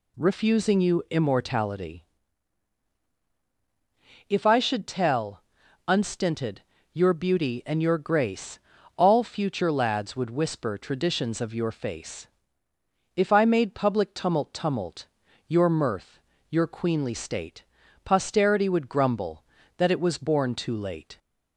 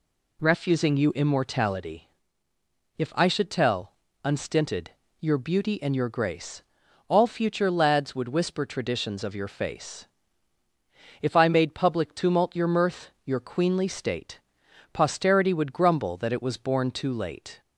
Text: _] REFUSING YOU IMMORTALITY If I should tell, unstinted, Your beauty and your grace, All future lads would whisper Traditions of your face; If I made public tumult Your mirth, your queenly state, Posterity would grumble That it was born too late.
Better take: second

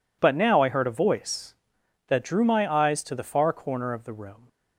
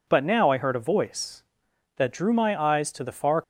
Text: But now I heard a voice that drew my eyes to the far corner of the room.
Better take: first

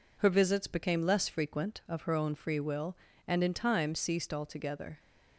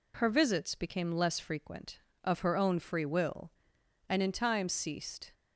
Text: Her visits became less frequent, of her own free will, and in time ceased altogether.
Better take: first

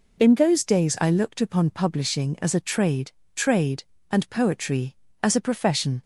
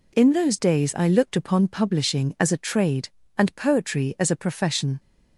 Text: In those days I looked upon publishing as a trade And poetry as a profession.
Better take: second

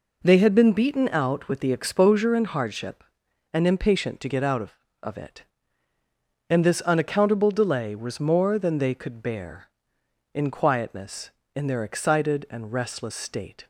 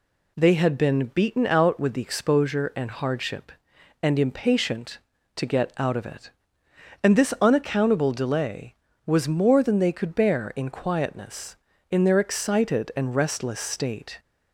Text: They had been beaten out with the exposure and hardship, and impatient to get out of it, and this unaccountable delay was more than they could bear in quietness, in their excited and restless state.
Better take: second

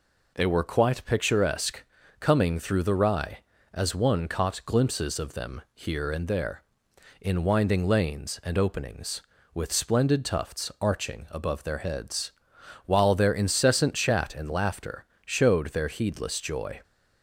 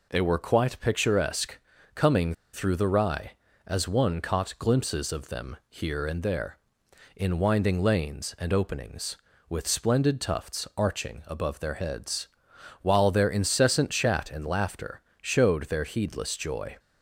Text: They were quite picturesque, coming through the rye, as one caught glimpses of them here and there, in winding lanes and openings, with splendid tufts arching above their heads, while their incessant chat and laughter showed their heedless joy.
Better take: first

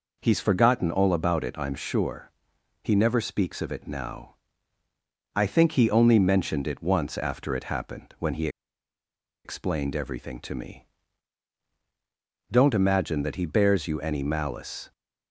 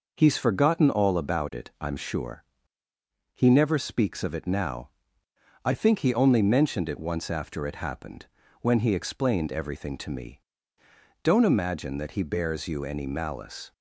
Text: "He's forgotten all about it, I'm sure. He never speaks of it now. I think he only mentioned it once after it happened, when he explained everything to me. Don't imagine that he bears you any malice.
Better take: second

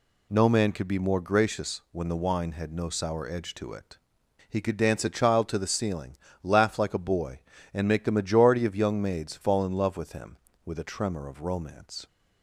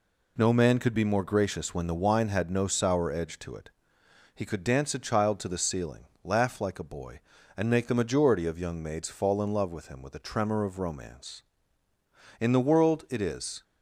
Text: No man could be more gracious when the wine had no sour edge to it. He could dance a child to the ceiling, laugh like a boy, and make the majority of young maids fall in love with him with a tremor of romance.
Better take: first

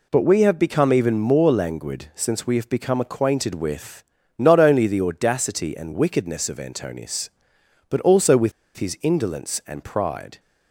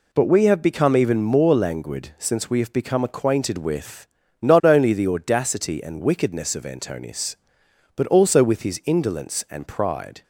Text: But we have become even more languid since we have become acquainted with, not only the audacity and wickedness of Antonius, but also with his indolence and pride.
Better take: second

